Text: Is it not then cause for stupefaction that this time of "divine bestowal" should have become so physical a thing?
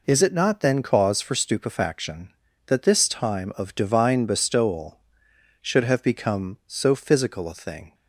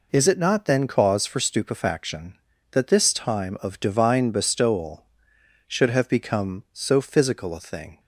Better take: neither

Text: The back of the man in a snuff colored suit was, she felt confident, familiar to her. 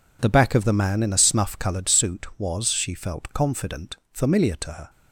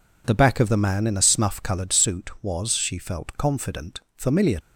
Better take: first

